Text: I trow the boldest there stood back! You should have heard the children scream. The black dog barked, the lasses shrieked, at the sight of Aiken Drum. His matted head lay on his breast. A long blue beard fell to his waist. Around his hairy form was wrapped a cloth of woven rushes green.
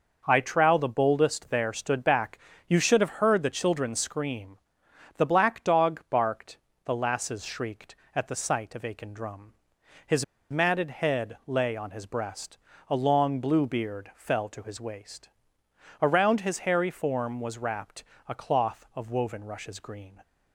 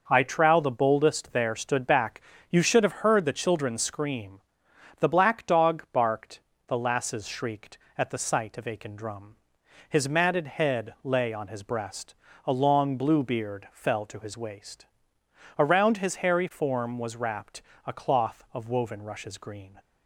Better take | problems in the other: second | pauses between "His" and "matted"; slight; at 10.2 s; 0.26 s long // pauses between "wrapped" and "a"; slight; at 18.0 s; 0.24 s long; slight in the second

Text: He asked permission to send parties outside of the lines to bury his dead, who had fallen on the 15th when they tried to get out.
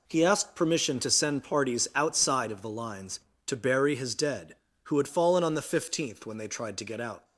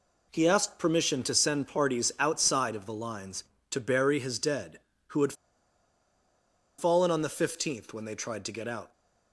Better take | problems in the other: first | pauses between "had" and "fallen"; strong; at 5.3 s; 1.4 s long

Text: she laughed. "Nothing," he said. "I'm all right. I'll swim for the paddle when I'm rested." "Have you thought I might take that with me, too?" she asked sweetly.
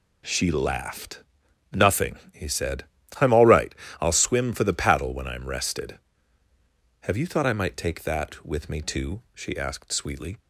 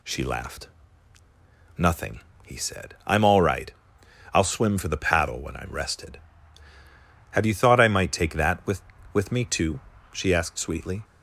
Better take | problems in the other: first | says "with" twice; at 9.1 s

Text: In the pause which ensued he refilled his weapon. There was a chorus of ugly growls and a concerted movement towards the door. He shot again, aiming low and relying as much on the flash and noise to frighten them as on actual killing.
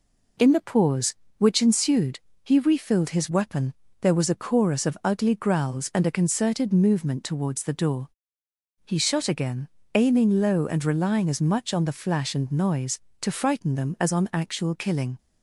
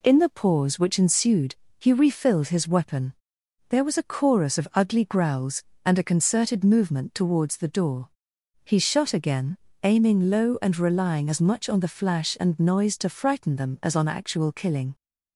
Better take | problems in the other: neither | pauses between "ensued" and "he"; slight; the same in both

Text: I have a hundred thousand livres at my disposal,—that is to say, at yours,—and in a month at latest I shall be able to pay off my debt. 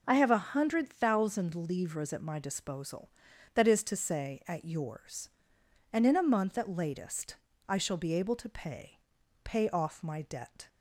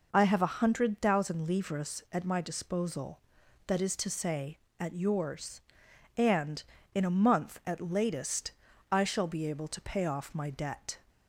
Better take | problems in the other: second | pauses between "latest" and "I"; slight; at 7.3 s; 0.34 s long; also in the second // says "pay" twice; at 9.4 s

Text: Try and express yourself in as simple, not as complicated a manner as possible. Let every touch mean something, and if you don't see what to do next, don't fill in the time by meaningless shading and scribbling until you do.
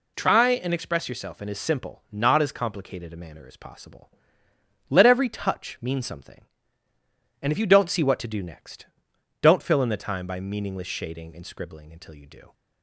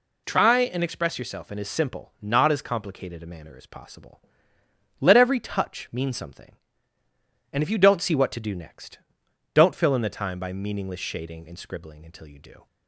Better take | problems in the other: neither | none

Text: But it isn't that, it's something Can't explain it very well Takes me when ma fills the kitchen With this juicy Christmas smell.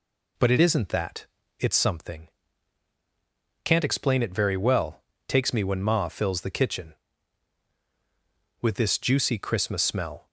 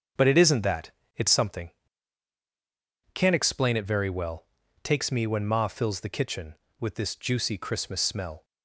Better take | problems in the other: first | gets quieter; strong; throughout; 9 dB // pauses between "something" and "Can't"; strong; at 1.7 s; 1.4 s long; strong in the first // pauses between "well" and "Takes"; at 4.4 s; 0.38 s long; slight in the first

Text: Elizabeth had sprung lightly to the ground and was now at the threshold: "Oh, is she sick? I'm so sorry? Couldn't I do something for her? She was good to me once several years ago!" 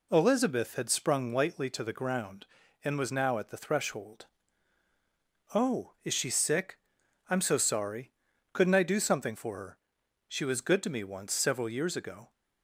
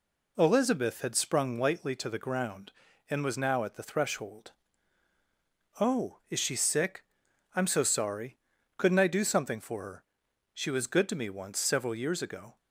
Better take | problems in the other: neither | none

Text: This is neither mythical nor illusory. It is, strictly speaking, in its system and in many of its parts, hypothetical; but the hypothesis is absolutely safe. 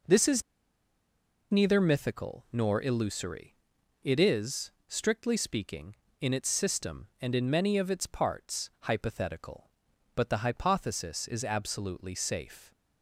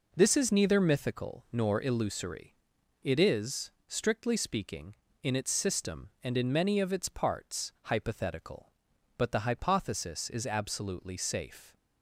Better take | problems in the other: second | pauses between "is" and "neither"; at 0.4 s; 1.0 s long

